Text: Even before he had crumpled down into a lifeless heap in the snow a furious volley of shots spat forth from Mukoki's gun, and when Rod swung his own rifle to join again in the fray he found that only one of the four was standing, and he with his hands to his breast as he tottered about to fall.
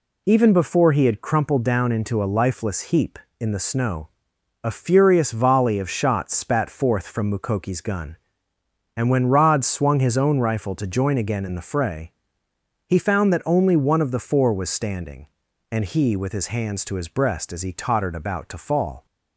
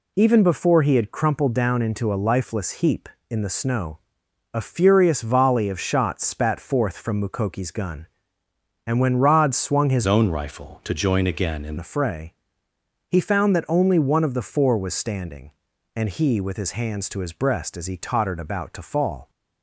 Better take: first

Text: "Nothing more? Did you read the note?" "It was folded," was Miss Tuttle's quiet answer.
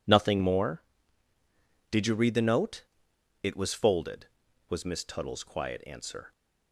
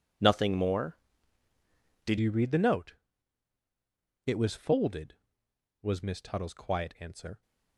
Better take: first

